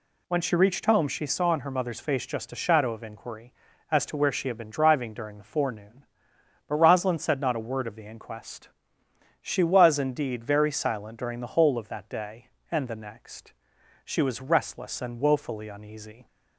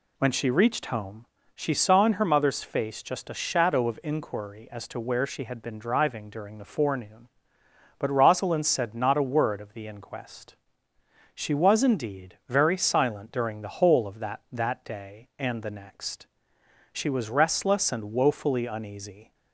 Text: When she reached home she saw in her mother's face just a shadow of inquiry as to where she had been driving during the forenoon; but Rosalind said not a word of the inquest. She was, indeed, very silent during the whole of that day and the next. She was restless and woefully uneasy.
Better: first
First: none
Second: pauses between "home" and "she"; slight; at 1.2 s; 0.32 s long // says "that" twice; at 14.5 s

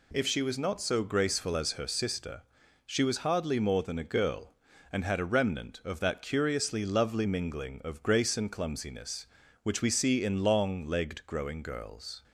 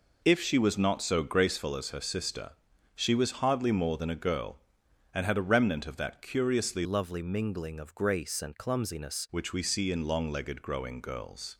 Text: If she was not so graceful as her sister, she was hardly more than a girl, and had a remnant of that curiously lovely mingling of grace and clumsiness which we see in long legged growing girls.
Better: first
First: none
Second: changes voice from "lovely" to "clumsiness"; from 6.8 to 9.2 s; 2.4 s long

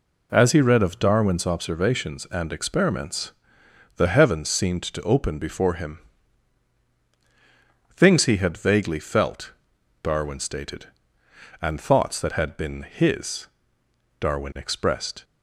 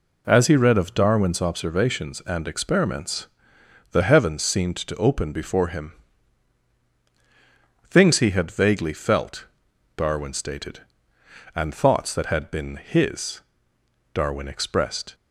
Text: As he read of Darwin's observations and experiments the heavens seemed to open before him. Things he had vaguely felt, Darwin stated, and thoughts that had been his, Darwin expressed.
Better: neither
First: pauses between "experiments" and "the"; noticeable; at 3.3 s; 0.64 s long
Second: pauses between "experiments" and "the"; noticeable; at 3.2 s; 0.64 s long

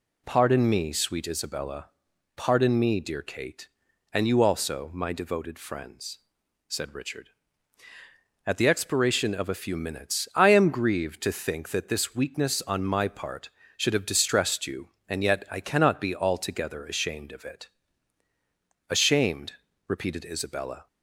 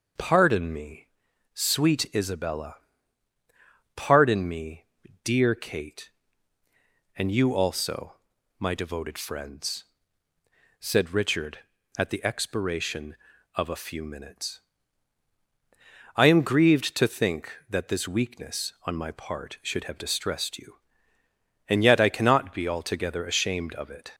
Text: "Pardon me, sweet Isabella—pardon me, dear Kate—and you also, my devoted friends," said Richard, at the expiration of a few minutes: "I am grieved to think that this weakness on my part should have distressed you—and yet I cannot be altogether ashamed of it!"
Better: second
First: goes on to say "Ashamed repeated Isabella"; strong; from 18.8 s on; 1.9 s long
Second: none

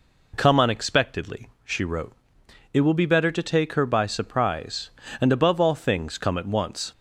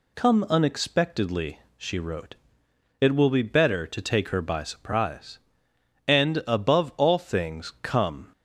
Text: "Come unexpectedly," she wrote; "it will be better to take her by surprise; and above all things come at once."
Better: first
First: none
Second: stops before "at once"; at 8.3 s

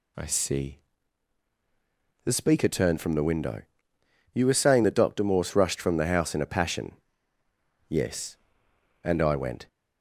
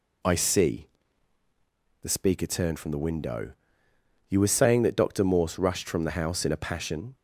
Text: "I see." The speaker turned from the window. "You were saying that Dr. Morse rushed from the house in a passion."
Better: second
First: goes on to say "Yes And I went"; strong; from 7.8 s on; 1.7 s long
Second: none

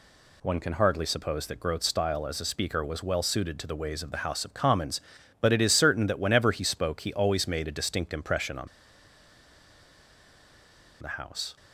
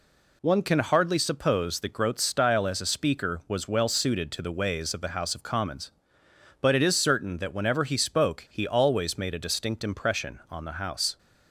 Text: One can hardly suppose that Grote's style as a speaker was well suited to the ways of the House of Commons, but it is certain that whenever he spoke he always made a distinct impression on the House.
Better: second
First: pauses between "on" and "the"; strong; at 8.6 s; 2.3 s long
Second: none

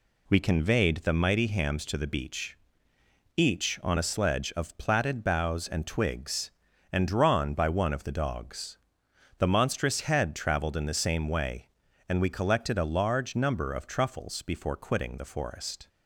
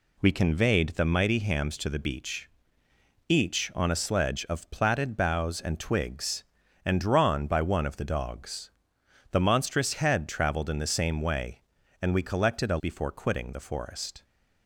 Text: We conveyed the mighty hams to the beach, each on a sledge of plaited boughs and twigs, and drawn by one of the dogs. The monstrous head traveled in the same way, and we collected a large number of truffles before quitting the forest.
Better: first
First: none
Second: skips "large number of truffles"; at 12.7 s

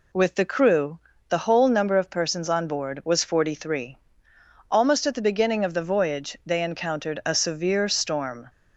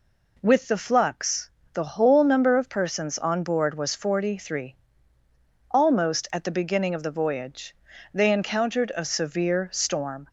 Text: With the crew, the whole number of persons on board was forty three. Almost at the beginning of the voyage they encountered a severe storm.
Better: first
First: none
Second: says "flux" for "crew"; at 0.7 s // pauses between "voyage" and "they"; at 7.7 s; 0.40 s long

